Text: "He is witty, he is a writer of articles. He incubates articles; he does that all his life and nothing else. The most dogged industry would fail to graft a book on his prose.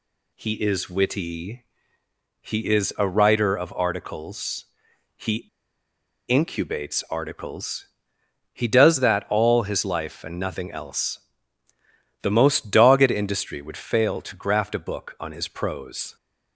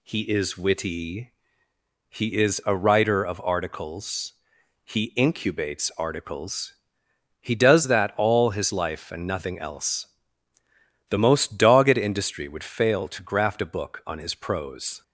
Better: second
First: pauses between "He" and "incubates"; noticeable; at 5.4 s; 0.81 s long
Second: none

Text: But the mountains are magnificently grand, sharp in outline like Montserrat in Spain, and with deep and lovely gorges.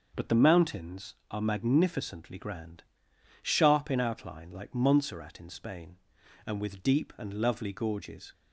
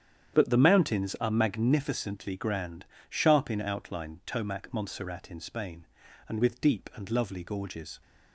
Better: first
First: starts louder than the rest; until 1.3 s; 6 dB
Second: starts louder than the rest; strong; until 1.4 s; 9 dB // says "tomac" for "like"; at 4.2 s

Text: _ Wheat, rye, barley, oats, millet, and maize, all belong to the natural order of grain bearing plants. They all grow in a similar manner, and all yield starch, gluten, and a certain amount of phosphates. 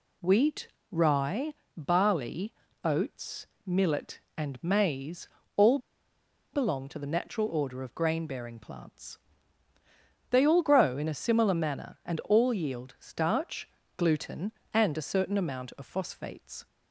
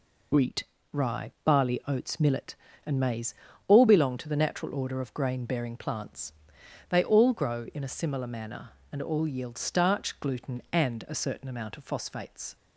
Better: second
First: pauses between "all" and "belong"; noticeable; at 5.7 s; 0.75 s long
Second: none

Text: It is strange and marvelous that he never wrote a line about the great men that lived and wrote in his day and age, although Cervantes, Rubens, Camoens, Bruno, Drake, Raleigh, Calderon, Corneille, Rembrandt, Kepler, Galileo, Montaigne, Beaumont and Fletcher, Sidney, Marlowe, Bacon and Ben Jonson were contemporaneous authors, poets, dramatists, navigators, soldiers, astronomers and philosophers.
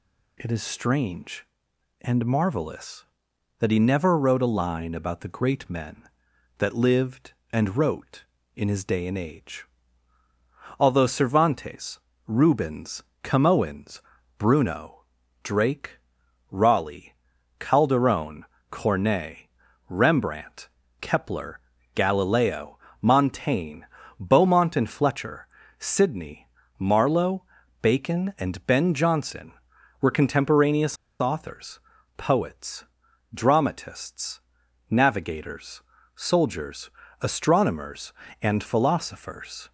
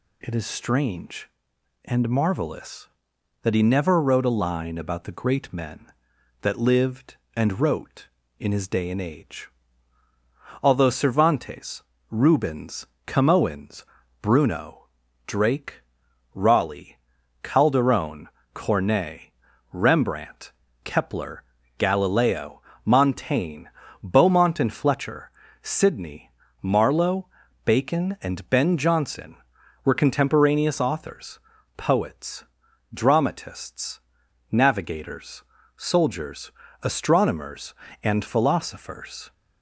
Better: second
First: pauses between "contemporaneous" and "authors"; slight; at 30.9 s; 0.24 s long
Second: none

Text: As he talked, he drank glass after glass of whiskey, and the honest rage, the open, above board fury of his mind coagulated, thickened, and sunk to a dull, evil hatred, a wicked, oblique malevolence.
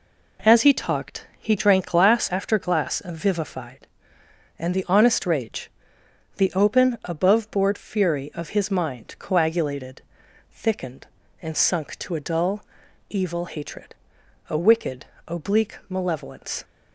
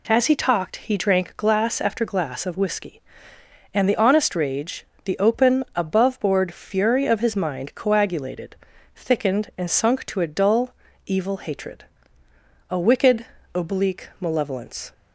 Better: second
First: says "vivified" for "whiskey"; at 3.1 s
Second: none

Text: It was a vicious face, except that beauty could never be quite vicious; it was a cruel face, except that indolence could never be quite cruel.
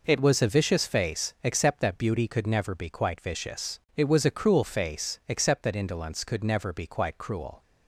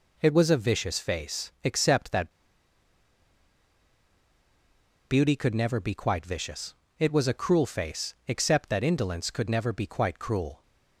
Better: first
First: none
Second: pauses between "that" and "beauty"; strong; at 2.3 s; 2.7 s long

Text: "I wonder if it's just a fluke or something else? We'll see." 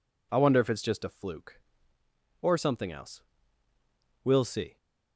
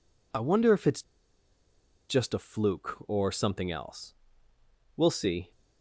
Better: first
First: none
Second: pauses between "it's" and "just"; at 1.0 s; 1.0 s long

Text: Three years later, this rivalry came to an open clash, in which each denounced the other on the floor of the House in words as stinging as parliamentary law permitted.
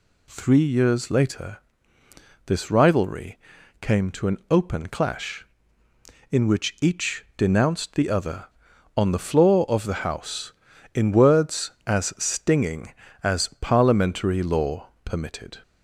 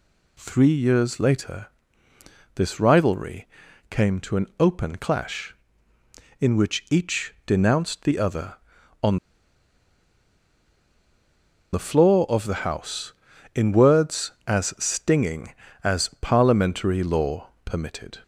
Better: first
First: pauses between "rivalry" and "came"; at 3.3 s; 0.42 s long // pauses between "law" and "permitted"; slight; at 14.8 s; 0.16 s long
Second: pauses between "rivalry" and "came"; at 3.4 s; 0.42 s long // pauses between "on" and "the"; strong; at 9.1 s; 2.5 s long // pauses between "law" and "permitted"; slight; at 17.4 s; 0.16 s long

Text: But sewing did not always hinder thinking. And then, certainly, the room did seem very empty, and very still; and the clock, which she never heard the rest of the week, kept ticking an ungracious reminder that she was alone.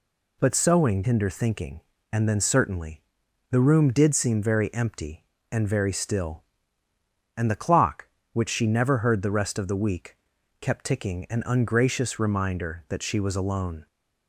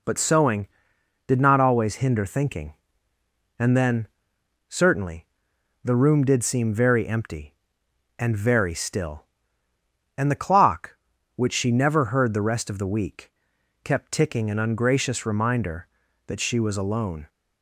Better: second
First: skips "did not always"; at 1.0 s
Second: none

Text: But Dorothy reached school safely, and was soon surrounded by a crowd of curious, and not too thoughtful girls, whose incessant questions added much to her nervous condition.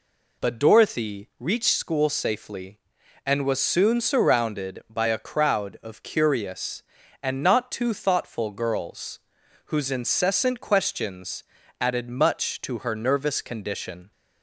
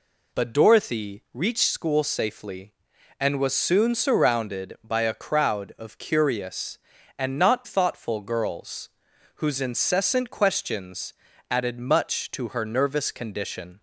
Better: first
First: pauses between "questions" and "added"; at 11.4 s; 0.38 s long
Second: skips "too"; at 7.6 s // pauses between "questions" and "added"; at 11.1 s; 0.38 s long

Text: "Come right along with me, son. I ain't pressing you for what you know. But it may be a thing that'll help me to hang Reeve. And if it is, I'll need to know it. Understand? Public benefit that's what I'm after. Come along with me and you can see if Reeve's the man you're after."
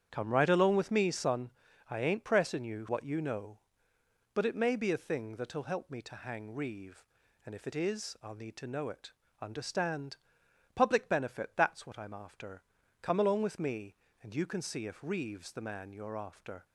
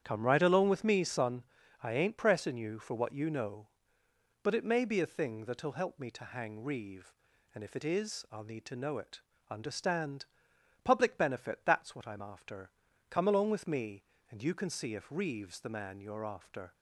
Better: second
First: starts louder than the rest; strong; until 1.1 s; 8.5 dB // skips "for"; at 2.8 s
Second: starts louder than the rest; strong; until 1.0 s; 9 dB

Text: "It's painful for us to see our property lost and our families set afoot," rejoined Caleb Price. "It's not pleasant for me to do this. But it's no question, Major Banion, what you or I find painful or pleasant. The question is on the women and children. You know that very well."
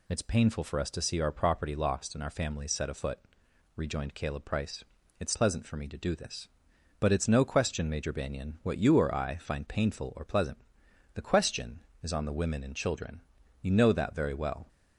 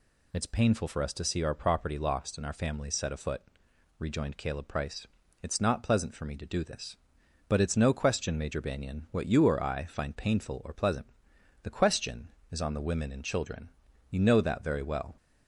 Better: second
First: skips "not"; at 5.3 s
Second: none

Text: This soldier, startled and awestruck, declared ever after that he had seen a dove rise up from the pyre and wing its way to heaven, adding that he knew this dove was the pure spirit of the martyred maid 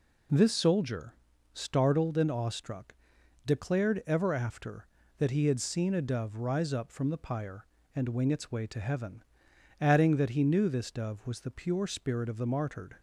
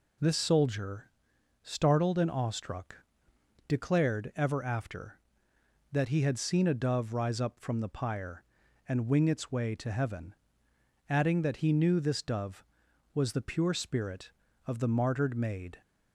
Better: second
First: stops before "maid"; at 12.9 s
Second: none

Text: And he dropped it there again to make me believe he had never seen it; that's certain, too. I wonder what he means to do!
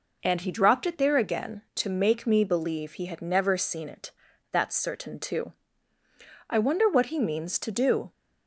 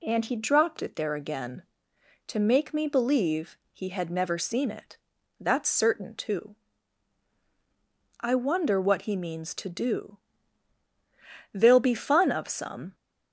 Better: first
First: none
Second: pauses between "believe" and "he"; slight; at 3.5 s; 0.16 s long // goes on to say "There'll be fun of some"; from 11.5 s on; 1.4 s long

